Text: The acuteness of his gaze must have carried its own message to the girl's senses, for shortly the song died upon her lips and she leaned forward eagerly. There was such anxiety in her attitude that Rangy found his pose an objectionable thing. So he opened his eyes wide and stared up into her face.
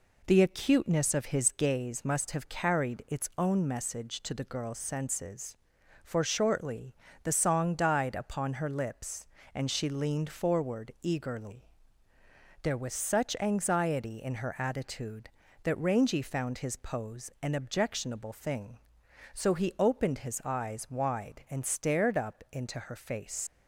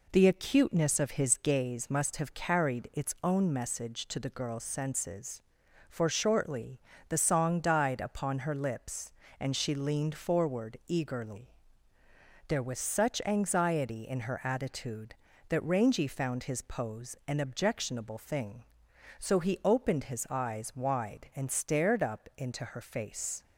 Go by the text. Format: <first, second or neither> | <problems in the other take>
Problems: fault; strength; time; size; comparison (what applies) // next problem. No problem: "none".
second | pauses between "shortly" and "the"; slight; at 6.9 s; 0.30 s long; slight in the second // leaves "face" unfinished; at 23.4 s; 105 ms